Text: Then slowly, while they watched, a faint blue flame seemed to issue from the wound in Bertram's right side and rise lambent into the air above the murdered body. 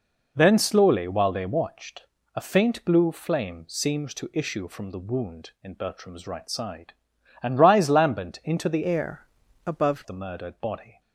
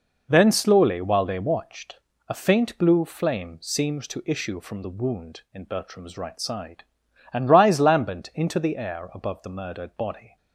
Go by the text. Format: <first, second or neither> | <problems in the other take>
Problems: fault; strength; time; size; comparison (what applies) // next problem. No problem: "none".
second | changes voice from "air" to "above"; from 8.8 to 10.0 s; 1.2 s long // pauses between "air" and "above"; at 9.2 s; 0.42 s long